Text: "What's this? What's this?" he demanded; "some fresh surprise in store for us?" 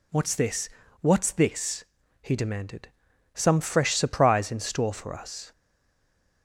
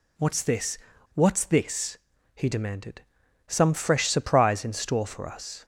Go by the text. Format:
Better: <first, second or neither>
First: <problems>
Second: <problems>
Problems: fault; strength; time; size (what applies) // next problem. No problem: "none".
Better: second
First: stays silent after the last word; slight; from 5.5 s on; 0.9 s long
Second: none